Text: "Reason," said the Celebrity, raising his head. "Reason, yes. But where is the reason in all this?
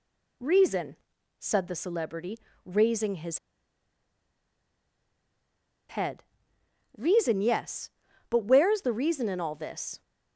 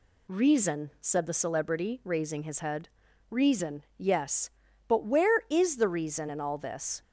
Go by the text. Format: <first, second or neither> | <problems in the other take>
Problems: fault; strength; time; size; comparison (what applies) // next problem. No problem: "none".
second | pauses between "his" and "head"; strong; at 3.3 s; 2.6 s long